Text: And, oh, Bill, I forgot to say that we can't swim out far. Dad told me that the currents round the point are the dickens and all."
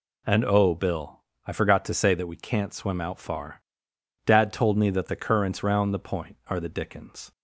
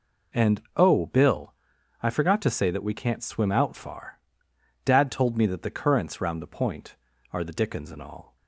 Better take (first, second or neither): second